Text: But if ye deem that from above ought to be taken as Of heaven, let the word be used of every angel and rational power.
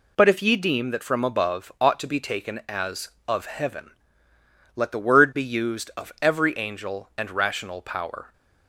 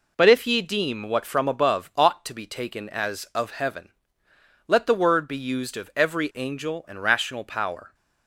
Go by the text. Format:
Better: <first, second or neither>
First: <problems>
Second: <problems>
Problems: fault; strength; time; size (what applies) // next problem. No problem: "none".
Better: first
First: none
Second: says "what" for "that"; at 1.0 s